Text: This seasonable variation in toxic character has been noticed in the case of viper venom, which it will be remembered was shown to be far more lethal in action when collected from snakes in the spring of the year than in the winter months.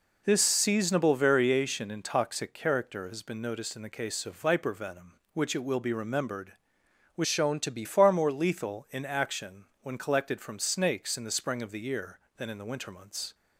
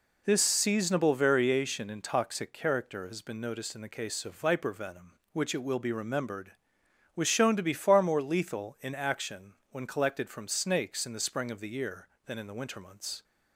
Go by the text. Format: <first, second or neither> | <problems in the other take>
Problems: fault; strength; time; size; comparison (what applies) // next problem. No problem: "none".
second | changes voice from "shown" to "be"; from 7.2 to 7.8 s; 0.6 s long // pauses between "action" and "when"; slight; at 9.6 s; 0.18 s long; slight in the second